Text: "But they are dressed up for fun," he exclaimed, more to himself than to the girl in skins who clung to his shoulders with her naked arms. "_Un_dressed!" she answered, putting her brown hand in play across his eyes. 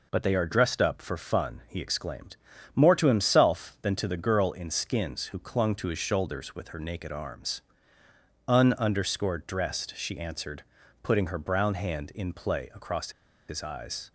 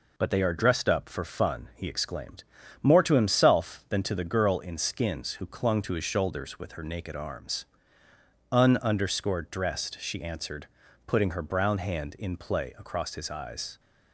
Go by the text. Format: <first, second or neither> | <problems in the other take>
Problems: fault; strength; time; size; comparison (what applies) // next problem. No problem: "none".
second | pauses between "across" and "his"; at 13.1 s; 0.36 s long